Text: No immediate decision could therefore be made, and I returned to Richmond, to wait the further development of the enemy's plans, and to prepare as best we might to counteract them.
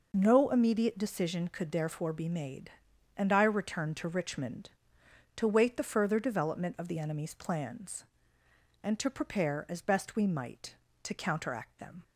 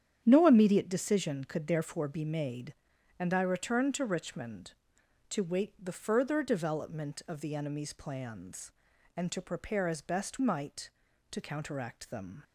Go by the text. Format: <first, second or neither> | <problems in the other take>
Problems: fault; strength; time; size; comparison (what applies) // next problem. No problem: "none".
first | starts louder than the rest; strong; until 1.2 s; 8.5 dB // skips "we"; at 10.3 s